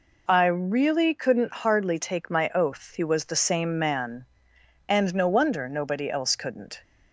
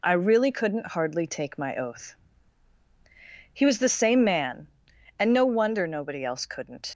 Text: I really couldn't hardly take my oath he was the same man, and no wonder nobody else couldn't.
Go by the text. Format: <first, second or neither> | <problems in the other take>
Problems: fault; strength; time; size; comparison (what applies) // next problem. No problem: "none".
first | pauses between "oath" and "he"; strong; at 2.1 s; 1.3 s long // leaves "couldn't" unfinished; at 6.8 s; 140 ms